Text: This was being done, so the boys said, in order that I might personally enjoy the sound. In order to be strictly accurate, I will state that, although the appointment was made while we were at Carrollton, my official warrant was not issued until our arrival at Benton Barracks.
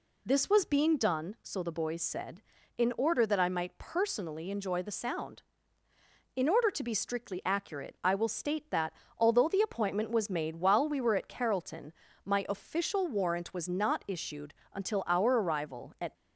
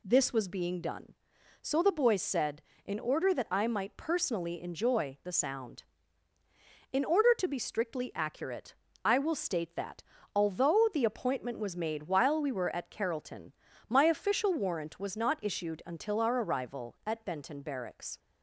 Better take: second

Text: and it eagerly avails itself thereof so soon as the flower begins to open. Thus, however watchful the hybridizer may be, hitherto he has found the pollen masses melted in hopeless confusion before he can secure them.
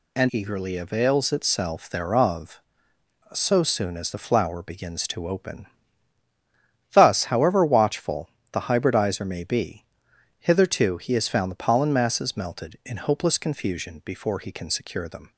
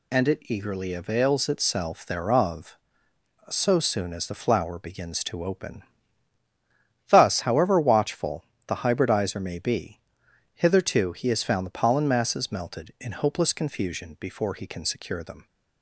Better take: second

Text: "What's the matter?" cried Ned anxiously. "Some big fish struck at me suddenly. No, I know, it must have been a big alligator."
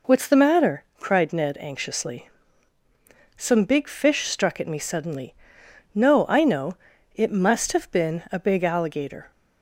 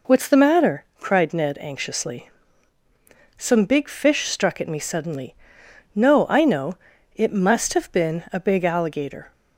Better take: neither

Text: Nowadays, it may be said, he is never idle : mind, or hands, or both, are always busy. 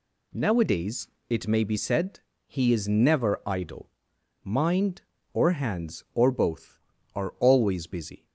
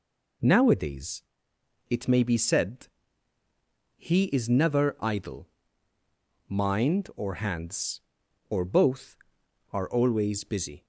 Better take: neither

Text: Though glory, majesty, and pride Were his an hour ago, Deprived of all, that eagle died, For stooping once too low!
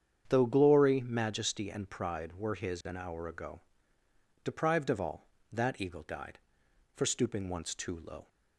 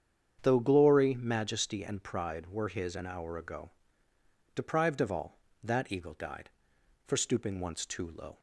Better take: neither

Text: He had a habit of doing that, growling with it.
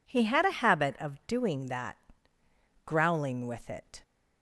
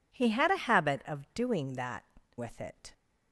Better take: first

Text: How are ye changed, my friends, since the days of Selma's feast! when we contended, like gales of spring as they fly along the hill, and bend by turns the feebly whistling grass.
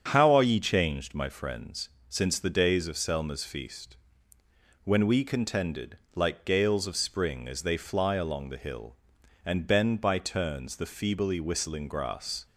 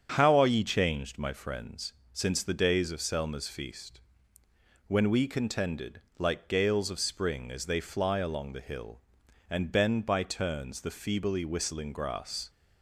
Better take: neither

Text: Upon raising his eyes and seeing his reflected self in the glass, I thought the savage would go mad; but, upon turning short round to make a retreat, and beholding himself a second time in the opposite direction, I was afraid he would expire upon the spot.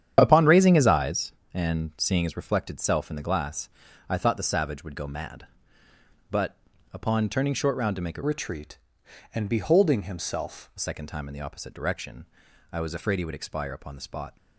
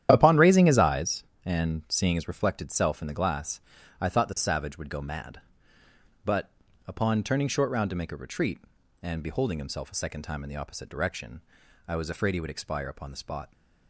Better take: second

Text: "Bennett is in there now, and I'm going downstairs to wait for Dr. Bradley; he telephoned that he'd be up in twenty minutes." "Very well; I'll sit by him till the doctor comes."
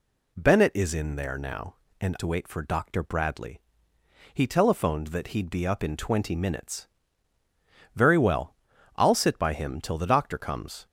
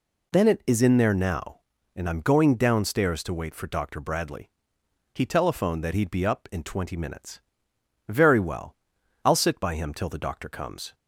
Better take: second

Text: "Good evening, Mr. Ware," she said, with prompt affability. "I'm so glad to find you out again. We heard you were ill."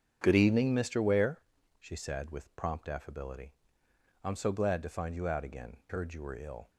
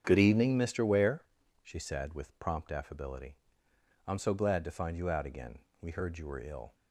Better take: second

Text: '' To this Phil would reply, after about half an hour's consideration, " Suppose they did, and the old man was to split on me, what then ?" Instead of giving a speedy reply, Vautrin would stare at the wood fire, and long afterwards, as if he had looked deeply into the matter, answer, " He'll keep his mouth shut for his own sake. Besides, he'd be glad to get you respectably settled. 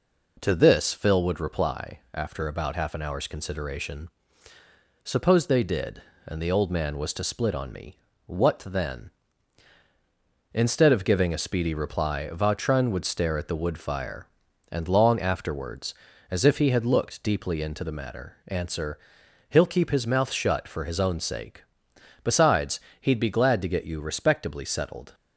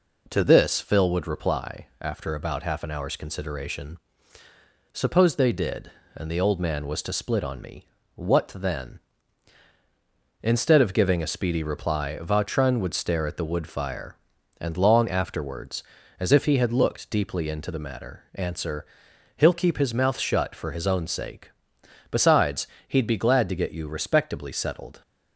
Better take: neither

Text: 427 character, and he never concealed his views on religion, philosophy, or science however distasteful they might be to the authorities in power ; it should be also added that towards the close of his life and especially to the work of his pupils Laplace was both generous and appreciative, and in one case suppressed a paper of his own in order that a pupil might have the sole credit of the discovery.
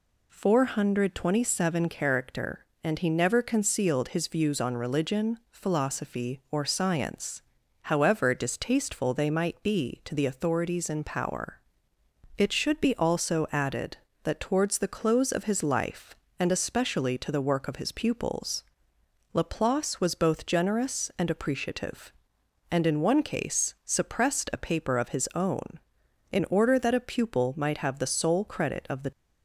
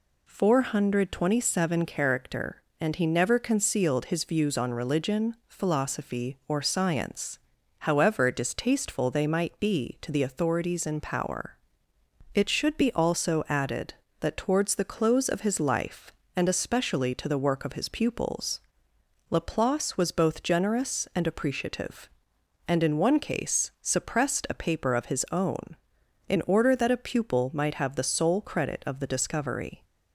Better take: second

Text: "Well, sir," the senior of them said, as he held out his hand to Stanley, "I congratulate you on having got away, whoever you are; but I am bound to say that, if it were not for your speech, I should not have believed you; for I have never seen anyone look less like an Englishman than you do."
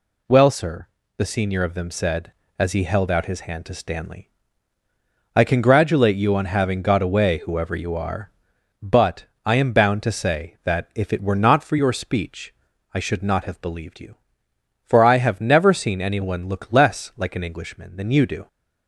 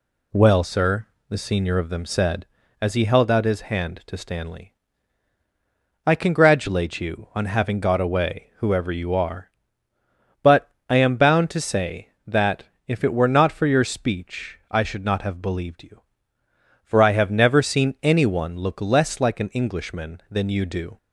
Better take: neither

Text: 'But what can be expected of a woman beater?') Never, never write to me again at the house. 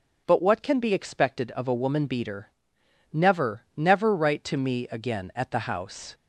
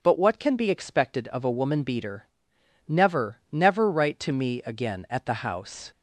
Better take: neither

